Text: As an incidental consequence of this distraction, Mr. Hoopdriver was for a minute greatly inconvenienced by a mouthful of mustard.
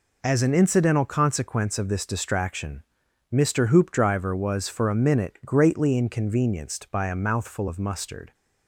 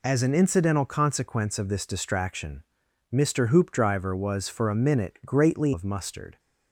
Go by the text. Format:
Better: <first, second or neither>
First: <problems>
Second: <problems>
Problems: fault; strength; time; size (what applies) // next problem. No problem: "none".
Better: first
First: none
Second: skips "inconvenienced by a mouthful"; at 5.7 s